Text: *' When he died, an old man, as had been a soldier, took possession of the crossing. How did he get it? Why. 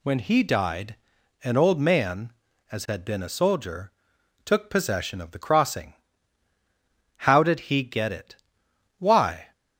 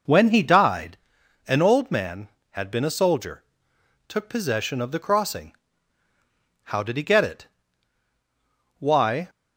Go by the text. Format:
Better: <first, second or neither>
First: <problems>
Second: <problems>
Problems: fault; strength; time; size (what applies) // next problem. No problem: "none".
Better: first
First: none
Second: skips "as"; at 2.3 s